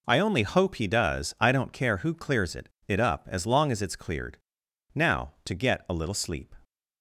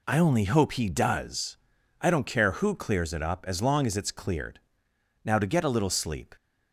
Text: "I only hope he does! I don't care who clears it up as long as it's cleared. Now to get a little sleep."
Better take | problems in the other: second | says "it" twice; at 2.8 s

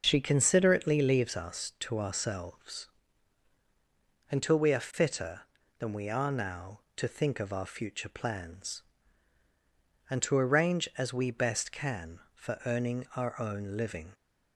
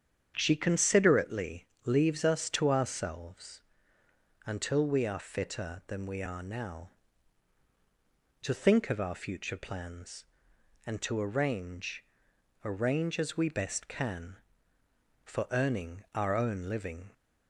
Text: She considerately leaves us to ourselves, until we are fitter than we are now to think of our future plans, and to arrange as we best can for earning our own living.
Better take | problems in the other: first | starts louder than the rest; strong; until 1.3 s; 8 dB // pauses between "considerately" and "leaves"; slight; at 1.6 s; 0.20 s long // says "arrange" twice; at 12.6 s

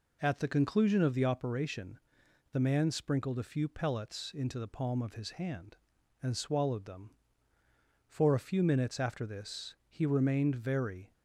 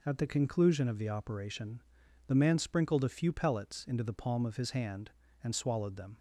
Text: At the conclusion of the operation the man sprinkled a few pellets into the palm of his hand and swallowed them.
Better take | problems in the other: second | pauses between "operation" and "the"; noticeable; at 1.9 s; 0.52 s long; also in the second // goes on to say "For a few minutes after this he remained very"; strong; from 8.0 s on; 3.0 s long

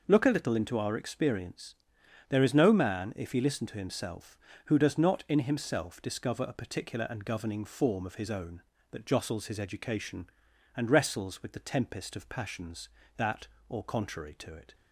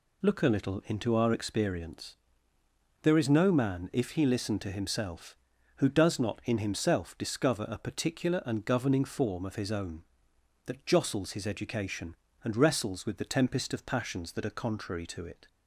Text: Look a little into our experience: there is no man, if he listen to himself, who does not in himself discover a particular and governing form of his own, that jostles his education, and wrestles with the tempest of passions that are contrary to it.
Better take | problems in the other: second | says "or" for "are"; at 13.6 s

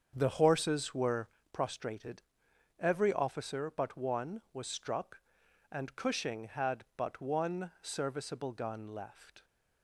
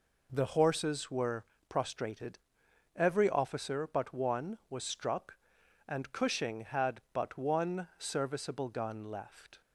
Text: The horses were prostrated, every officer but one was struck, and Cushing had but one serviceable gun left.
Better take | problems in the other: second | starts louder than the rest; strong; until 1.5 s; 7 dB // pauses between "were" and "prostrated"; slight; at 1.2 s; 0.26 s long; slight in the second

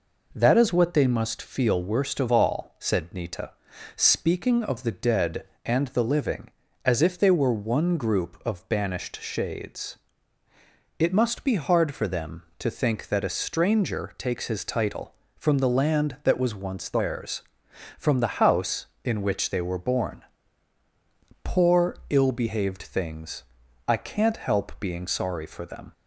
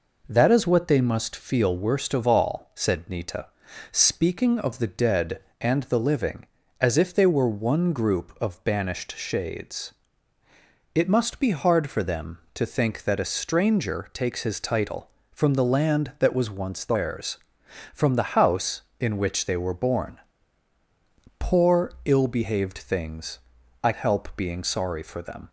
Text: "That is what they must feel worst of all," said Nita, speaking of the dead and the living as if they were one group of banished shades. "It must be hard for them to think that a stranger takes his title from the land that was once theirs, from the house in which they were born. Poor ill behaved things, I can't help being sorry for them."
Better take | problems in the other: first | skips "can't"; at 23.9 s

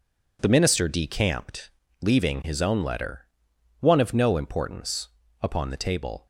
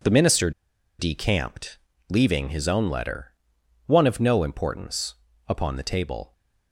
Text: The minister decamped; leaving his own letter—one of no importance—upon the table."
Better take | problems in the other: first | pauses between "minister" and "decamped"; noticeable; at 0.5 s; 0.48 s long

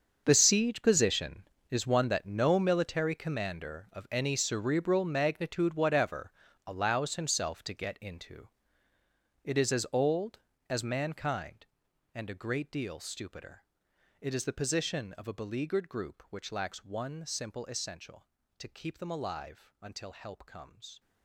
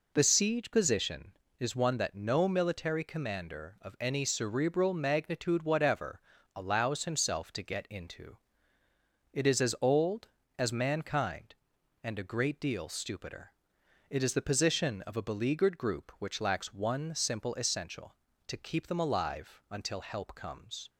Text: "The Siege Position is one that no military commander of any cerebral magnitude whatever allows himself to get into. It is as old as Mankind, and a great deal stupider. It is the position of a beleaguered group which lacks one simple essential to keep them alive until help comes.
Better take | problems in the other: second | gets quieter; strong; throughout; 15.5 dB // pauses between "whatever" and "allows"; slight; at 6.2 s; 0.36 s long; slight in the second

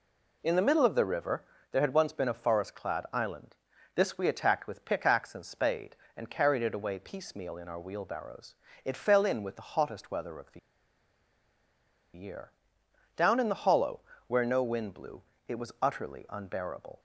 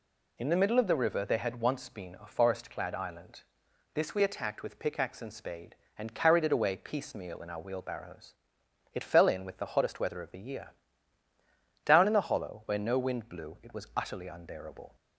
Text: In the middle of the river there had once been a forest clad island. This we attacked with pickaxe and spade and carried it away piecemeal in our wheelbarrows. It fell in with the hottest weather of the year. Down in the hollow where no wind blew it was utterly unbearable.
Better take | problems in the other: second | pauses between "river" and "there"; slight; at 1.4 s; 0.28 s long // pauses between "the" and "year"; strong; at 10.5 s; 1.5 s long // pauses between "hollow" and "where"; slight; at 13.9 s; 0.26 s long // pauses between "blew" and "it"; slight; at 15.2 s; 0.26 s long

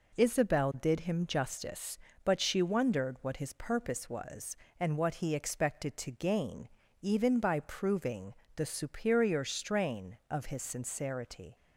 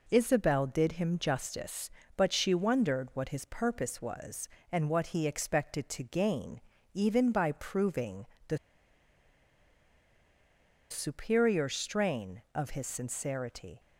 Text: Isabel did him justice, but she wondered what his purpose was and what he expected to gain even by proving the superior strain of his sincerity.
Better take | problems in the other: first | pauses between "gain" and "even"; slight; at 6.6 s; 0.32 s long; slight in the first // pauses between "proving" and "the"; slight; at 8.2 s; 0.22 s long; slight in the first // pauses between "the" and "superior"; strong; at 8.5 s; 2.3 s long

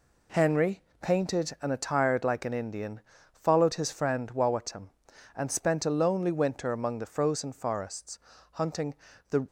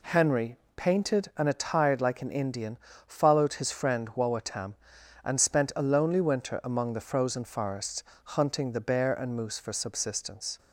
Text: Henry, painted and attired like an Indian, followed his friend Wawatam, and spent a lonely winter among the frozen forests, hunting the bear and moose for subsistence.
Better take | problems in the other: second | pauses between "hunting" and "the"; slight; at 8.9 s; 0.36 s long // stops before "bear and moose for subsistence"; at 9.4 s

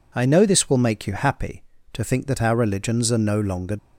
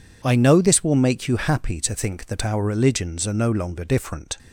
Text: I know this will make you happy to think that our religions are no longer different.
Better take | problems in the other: second | stops before "different"; at 3.7 s

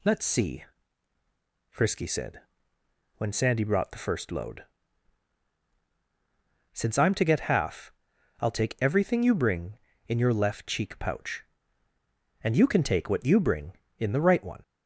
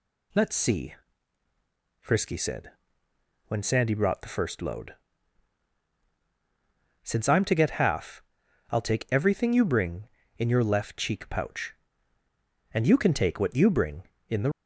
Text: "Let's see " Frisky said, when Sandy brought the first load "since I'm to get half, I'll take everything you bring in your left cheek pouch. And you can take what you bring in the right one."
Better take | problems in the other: first | pauses between "load" and "since"; strong; at 4.9 s; 2.0 s long; strong in the first // stops before "right one"; at 14.5 s

